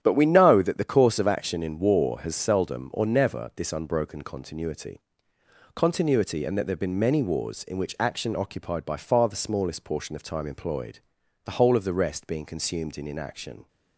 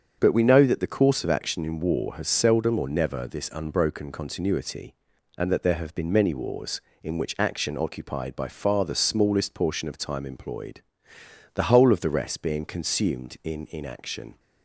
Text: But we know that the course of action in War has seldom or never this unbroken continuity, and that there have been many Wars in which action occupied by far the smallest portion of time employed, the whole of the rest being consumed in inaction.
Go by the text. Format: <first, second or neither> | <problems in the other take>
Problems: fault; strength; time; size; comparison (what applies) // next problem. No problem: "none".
second | starts louder than the rest; strong; until 1.0 s; 9.5 dB; strong in the second // says "continuity" twice; at 5.7 s